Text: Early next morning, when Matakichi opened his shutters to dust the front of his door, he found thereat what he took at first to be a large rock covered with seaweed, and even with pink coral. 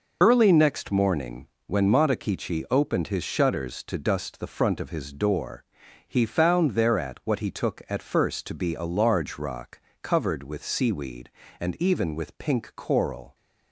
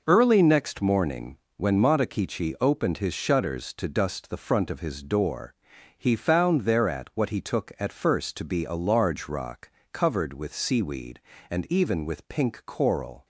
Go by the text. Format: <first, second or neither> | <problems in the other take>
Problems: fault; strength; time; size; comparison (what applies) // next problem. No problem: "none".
second | loses the start of "Early"; at 0.2 s; 60 ms // pauses between "rock" and "covered"; slight; at 9.8 s; 0.22 s long; slight in the second